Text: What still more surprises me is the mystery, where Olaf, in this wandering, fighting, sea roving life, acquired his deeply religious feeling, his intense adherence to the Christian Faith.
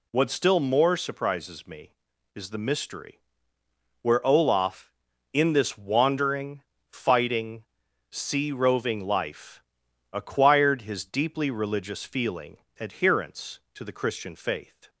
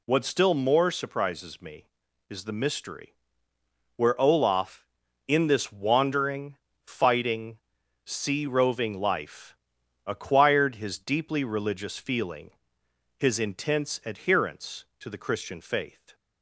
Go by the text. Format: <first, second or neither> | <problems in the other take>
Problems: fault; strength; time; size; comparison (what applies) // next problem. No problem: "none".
second | skips "his intense"; at 12.6 s